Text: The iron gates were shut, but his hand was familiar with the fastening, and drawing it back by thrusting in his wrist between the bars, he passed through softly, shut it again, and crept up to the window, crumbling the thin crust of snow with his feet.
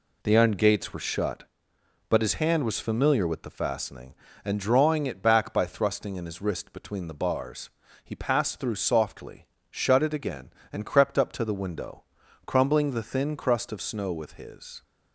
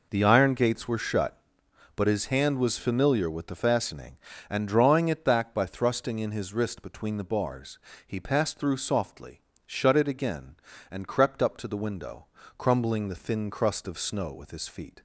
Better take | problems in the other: second | stops before "feet"; at 14.8 s

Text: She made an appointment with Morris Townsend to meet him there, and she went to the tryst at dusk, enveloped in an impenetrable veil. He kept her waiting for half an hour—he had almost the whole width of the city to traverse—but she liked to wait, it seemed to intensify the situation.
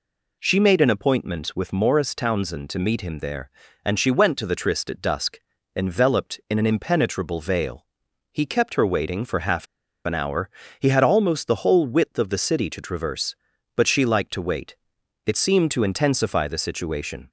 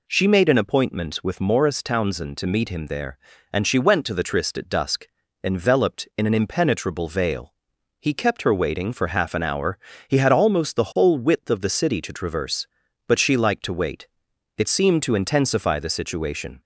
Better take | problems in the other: second | pauses between "half" and "an"; at 9.6 s; 0.39 s long

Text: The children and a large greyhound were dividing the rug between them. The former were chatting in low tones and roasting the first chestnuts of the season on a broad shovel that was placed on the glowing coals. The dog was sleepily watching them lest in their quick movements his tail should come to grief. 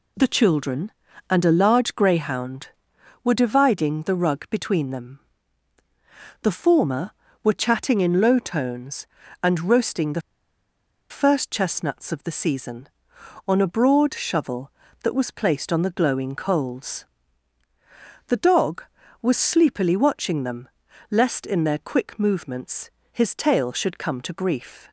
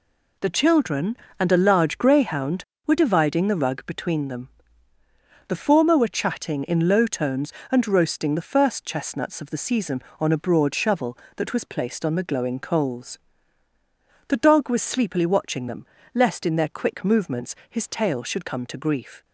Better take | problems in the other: second | pauses between "the" and "first"; noticeable; at 10.2 s; 0.90 s long // pauses between "them" and "lest"; at 20.6 s; 0.40 s long; slight in the second // pauses between "movements" and "his"; slight; at 22.8 s; 0.22 s long; slight in the second

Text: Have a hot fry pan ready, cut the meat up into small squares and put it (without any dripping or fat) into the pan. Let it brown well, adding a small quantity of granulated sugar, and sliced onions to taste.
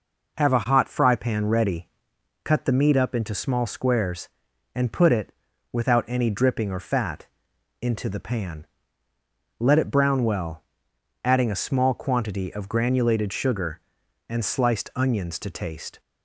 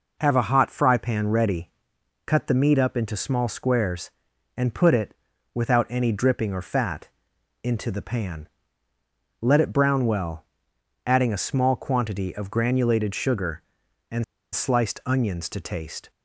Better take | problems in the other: first | pauses between "and" and "sliced"; slight; at 14.2 s; 0.29 s long

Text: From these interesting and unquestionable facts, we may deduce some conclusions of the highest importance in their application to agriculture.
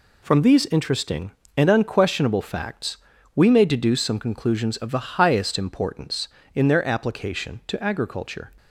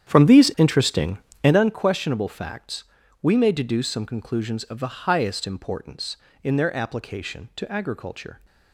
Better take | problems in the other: first | starts louder than the rest; strong; until 1.7 s; 9.5 dB

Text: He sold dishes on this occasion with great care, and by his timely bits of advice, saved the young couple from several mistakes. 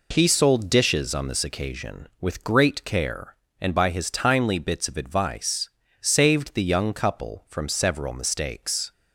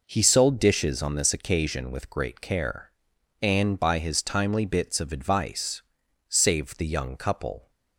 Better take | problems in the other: first | stops before "from several mistakes"; at 7.6 s

